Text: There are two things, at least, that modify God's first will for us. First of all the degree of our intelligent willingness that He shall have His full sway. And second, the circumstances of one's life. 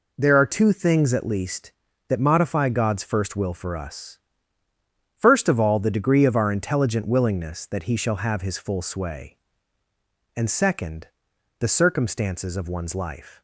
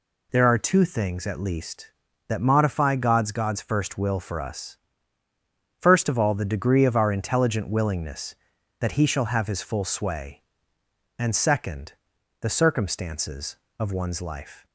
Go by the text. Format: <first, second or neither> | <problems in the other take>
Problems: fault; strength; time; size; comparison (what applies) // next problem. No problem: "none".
first | says "God's" twice; at 3.3 s